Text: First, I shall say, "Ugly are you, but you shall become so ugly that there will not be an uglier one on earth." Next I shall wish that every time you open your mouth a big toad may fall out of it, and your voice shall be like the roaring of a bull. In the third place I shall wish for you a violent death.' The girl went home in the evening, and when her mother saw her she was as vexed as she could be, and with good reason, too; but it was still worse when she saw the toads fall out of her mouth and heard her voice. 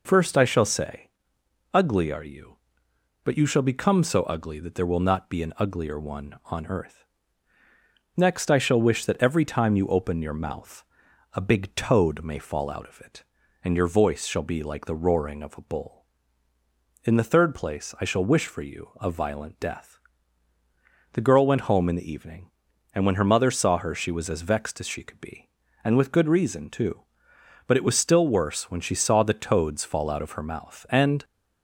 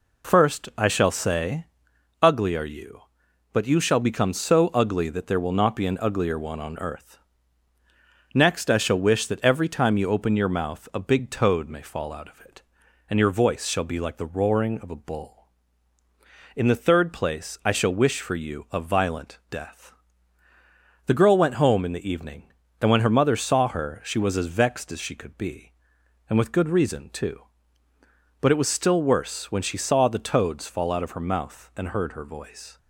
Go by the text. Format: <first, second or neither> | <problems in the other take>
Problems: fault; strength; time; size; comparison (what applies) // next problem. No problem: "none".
second | pauses between "mouth" and "a"; noticeable; at 10.8 s; 0.48 s long // stops before "heard her voice"; at 31.2 s